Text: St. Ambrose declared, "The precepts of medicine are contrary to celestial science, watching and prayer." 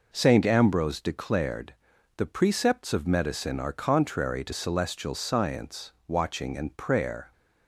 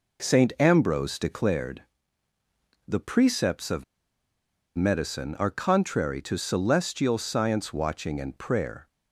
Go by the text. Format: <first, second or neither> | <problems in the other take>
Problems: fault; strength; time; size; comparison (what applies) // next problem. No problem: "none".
first | pauses between "of" and "medicine"; noticeable; at 3.8 s; 0.93 s long